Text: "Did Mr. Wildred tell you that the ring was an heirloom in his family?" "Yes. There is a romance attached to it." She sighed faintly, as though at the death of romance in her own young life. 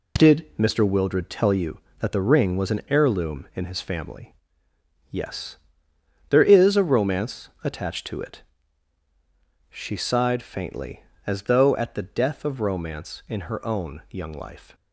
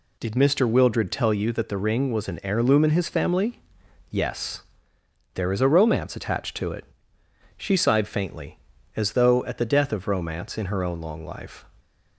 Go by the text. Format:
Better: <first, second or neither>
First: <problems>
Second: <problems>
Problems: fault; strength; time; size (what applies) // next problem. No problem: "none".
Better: first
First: none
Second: says "long" for "young"; at 10.9 s